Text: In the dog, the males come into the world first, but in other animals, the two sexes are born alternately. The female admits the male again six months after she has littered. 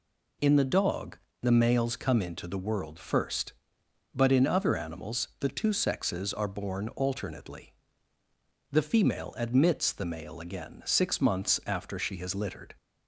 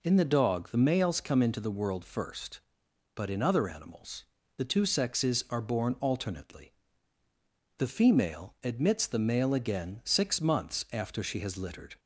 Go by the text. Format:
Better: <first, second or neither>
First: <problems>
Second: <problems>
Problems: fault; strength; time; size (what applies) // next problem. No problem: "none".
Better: neither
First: none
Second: none